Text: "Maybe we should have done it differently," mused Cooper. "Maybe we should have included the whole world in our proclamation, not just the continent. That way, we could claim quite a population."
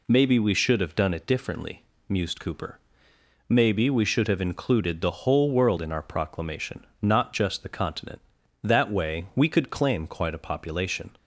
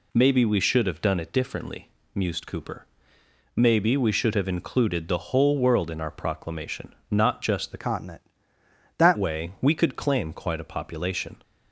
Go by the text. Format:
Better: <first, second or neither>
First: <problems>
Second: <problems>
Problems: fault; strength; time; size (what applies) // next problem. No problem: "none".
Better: first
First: none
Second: changes voice from "continent" to "That"; from 7.7 to 9.1 s; 1.4 s long